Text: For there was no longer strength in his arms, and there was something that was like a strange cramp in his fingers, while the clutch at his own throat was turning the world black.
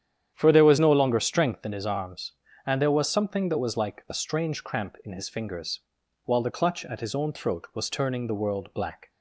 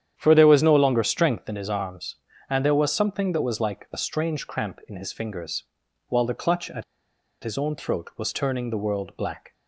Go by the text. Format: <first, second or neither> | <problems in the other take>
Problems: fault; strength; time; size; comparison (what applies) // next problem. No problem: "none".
first | starts louder than the rest; strong; until 1.1 s; 9.5 dB; strong in the first // pauses between "at" and "his"; noticeable; at 6.8 s; 0.60 s long